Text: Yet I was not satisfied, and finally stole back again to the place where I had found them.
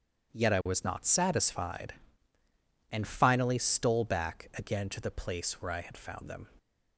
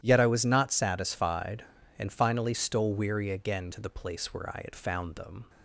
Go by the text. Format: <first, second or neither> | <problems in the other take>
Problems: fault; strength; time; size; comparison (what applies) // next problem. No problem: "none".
first | starts louder than the rest; strong; until 1.0 s; 11.5 dB; strong in the first // says "weary" for "back"; at 2.9 s